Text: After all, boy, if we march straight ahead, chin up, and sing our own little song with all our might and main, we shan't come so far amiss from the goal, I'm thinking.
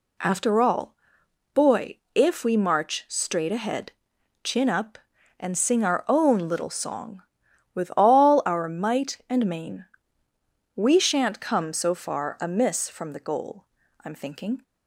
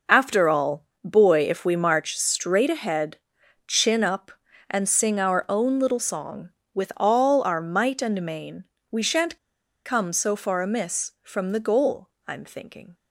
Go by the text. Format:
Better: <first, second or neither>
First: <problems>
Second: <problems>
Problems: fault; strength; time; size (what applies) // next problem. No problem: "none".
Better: first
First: none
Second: pauses between "shan't" and "come"; noticeable; at 9.3 s; 0.48 s long